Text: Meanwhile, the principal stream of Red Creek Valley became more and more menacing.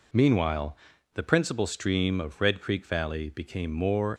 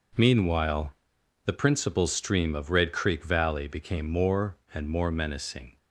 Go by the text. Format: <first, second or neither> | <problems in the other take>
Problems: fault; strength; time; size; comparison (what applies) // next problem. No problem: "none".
second | stops before "and more menacing"; at 4.1 s